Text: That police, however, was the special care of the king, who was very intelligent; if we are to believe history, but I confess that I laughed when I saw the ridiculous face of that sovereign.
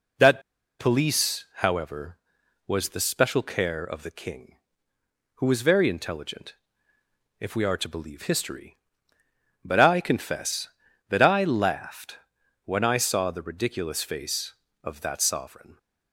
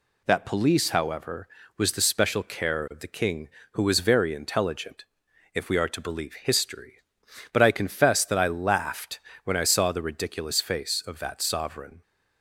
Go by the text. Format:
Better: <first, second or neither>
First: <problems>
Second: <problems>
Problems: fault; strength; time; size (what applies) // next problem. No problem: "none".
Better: second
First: pauses between "That" and "police"; at 0.4 s; 0.37 s long // pauses between "laughed" and "when"; noticeable; at 12.1 s; 0.48 s long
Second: pauses between "laughed" and "when"; slight; at 9.1 s; 0.24 s long